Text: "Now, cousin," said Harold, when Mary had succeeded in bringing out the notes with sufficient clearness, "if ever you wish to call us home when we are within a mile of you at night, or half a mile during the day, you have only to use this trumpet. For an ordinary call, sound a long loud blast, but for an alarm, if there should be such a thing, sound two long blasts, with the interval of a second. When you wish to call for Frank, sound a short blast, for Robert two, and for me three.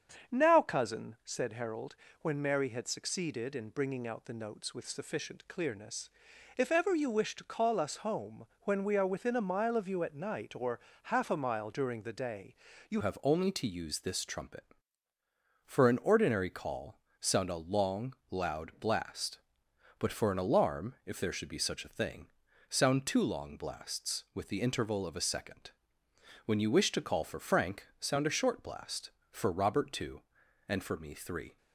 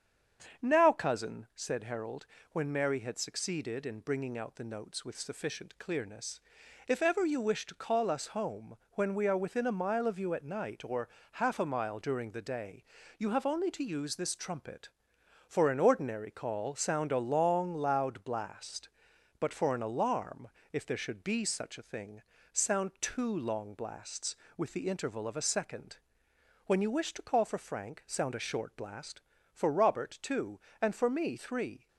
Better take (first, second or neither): second